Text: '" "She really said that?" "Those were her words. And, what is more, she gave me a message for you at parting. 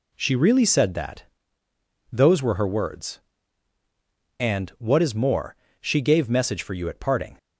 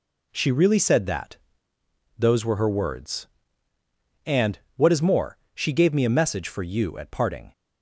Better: second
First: skips "me a"; at 6.2 s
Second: none

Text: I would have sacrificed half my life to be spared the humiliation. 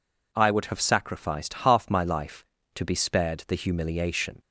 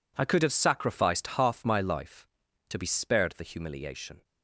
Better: first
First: none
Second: says "could" for "would"; at 0.2 s

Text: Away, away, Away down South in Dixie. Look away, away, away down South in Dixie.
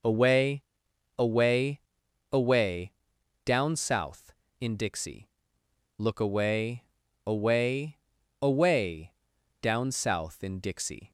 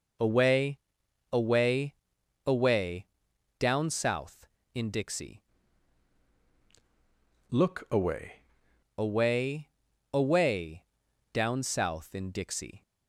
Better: first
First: pauses between "Away" and "down"; noticeable; at 2.9 s; 0.52 s long // pauses between "away" and "down"; noticeable; at 9.1 s; 0.48 s long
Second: pauses between "Away" and "down"; noticeable; at 3.0 s; 0.52 s long // changes voice from "Look" to "away"; from 7.5 to 8.4 s; 0.9 s long // pauses between "away" and "down"; noticeable; at 10.8 s; 0.48 s long

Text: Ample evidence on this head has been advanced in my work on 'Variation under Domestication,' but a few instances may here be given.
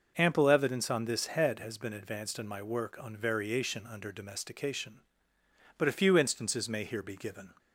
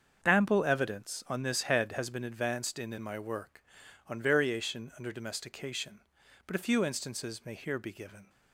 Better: first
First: none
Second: starts louder than the rest; until 1.2 s; 7 dB // says "in" twice; at 2.9 s

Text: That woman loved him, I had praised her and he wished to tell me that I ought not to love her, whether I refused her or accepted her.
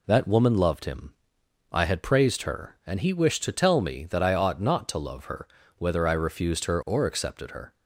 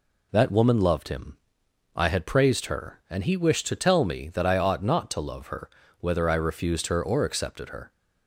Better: neither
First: none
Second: none

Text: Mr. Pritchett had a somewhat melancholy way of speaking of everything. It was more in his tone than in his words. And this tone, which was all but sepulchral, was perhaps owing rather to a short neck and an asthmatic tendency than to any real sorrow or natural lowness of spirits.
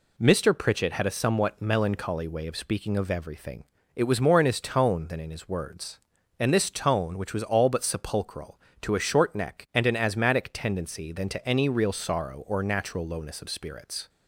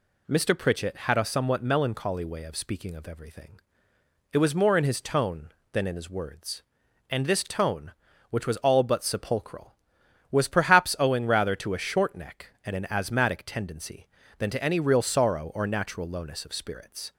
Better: second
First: skips "was perhaps owing rather"; at 8.7 s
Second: none

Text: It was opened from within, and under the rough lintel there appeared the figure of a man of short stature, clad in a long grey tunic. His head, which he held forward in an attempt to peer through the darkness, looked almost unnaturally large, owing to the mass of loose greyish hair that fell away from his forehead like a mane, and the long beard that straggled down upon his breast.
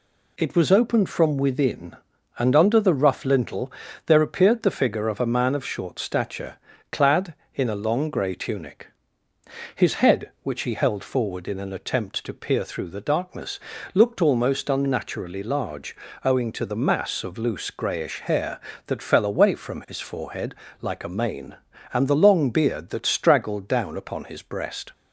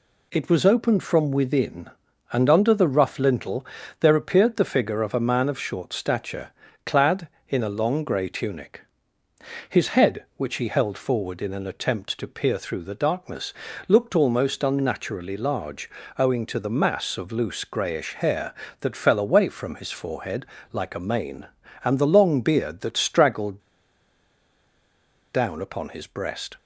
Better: first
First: pauses between "lintel" and "there"; slight; at 3.7 s; 0.36 s long // pauses between "forehead" and "like"; slight; at 20.5 s; 0.28 s long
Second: pauses between "lintel" and "there"; slight; at 3.6 s; 0.36 s long // pauses between "forehead" and "like"; slight; at 20.4 s; 0.28 s long // pauses between "straggled" and "down"; strong; at 23.5 s; 1.7 s long

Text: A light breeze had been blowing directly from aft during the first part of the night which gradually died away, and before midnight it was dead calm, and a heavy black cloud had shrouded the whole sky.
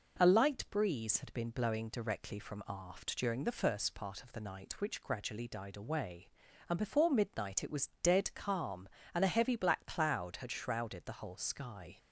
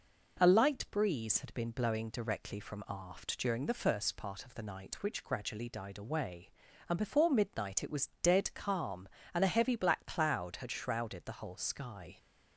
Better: neither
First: none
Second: none

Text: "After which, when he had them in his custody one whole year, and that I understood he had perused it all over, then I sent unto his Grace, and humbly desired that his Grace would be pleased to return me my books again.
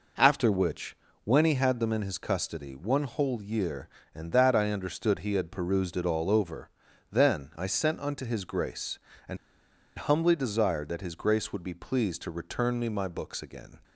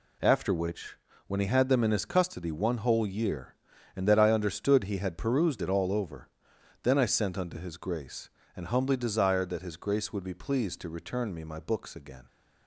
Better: second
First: pauses between "and" and "humbly"; noticeable; at 9.3 s; 0.61 s long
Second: none

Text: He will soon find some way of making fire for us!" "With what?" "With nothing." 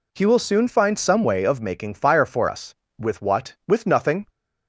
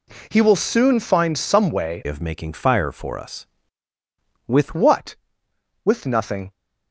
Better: first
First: none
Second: changes voice from "of" to "With"; from 2.0 to 4.7 s; 2.7 s long

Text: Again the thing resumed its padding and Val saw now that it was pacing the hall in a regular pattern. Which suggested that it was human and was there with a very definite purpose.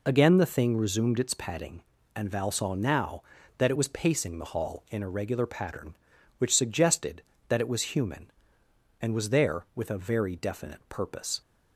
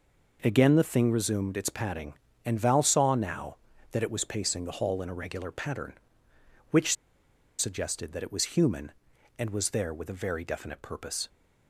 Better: first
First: none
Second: pauses between "Which" and "suggested"; noticeable; at 6.9 s; 0.64 s long

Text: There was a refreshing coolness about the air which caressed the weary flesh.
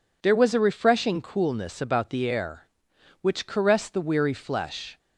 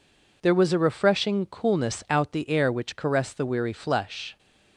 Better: first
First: none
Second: says "out" for "about"; at 2.0 s

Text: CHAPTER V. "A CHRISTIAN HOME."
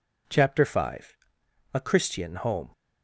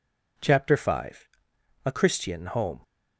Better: neither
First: none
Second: none

